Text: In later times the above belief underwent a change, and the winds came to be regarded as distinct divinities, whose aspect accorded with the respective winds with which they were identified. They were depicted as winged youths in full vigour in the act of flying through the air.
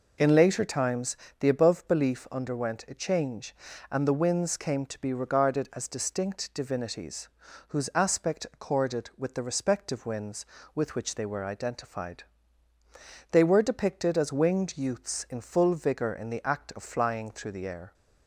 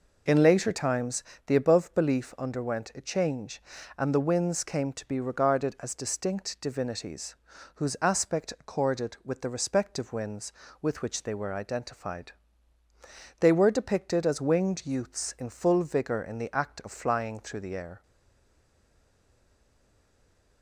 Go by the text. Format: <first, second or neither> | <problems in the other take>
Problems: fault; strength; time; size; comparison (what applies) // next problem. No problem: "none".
first | pauses between "times" and "the"; slight; at 1.2 s; 0.24 s long; slight in the first // stays silent after the last word; strong; from 18.0 s on; 2.6 s long